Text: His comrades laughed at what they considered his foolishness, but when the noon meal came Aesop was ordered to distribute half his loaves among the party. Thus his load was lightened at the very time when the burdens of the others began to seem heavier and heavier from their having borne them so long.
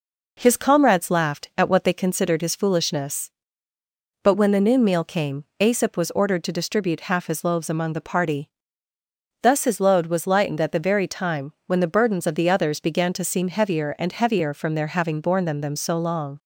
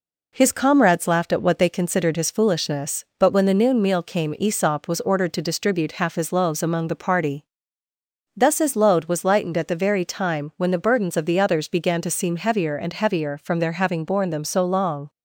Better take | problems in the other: second | pauses between "came" and "Aesop"; slight; at 5.4 s; 0.16 s long // says "them" twice; at 15.6 s

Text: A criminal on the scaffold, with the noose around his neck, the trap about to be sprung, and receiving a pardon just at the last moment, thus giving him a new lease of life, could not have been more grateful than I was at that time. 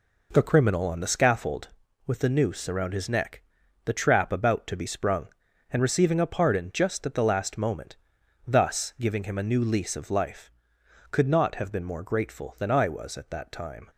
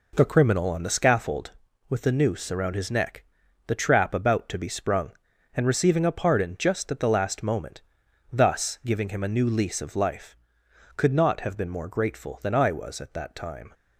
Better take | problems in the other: neither | none

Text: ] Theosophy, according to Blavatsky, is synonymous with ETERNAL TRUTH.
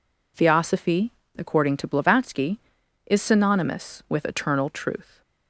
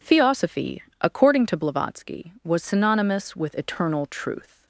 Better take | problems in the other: first | says "was" for "is"; at 2.4 s

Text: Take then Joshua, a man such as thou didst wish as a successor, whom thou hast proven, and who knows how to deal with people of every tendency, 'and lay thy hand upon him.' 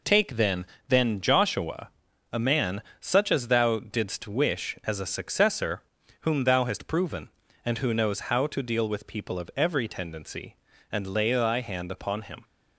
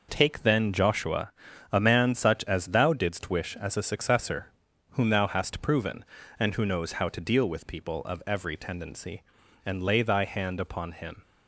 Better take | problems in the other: second | says "then" twice; at 0.8 s // pauses between "man" and "such"; slight; at 2.8 s; 0.18 s long

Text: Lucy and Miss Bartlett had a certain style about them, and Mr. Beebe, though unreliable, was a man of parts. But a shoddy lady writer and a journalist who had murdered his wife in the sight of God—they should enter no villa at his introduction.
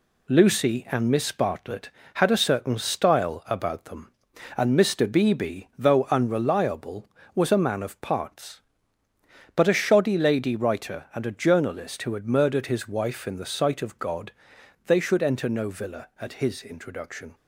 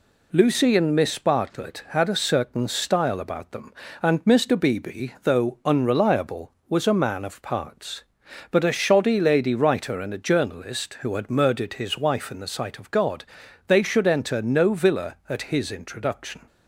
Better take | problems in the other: second | gets quieter; noticeable; throughout; 5 dB

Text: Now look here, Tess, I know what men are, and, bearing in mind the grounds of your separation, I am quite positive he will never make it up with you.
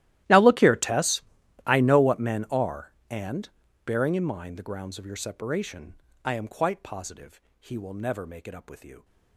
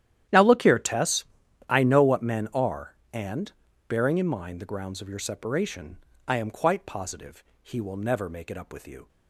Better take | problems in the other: second | gets quieter; strong; throughout; 23 dB // starts louder than the rest; strong; until 1.7 s; 15 dB; strong in the second // pauses between "positive" and "he"; slight; at 7.4 s; 0.20 s long; slight in the second

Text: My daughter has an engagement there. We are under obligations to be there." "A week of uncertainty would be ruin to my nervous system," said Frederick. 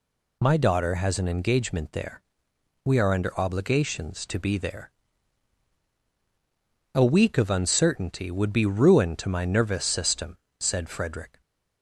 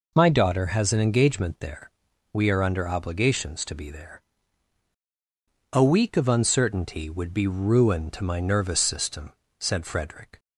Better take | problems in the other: neither | none

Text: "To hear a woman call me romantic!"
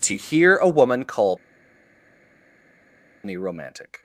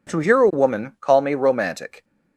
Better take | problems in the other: second | pauses between "call" and "me"; strong; at 1.3 s; 1.8 s long

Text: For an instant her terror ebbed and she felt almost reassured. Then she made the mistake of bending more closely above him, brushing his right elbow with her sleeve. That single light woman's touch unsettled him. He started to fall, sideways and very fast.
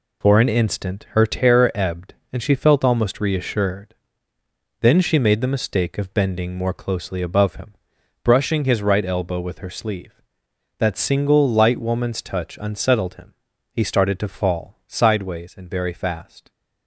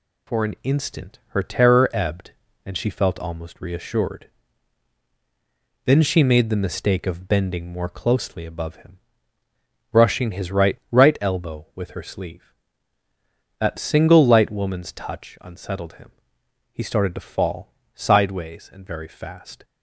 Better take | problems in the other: first | says "right" twice; at 10.9 s

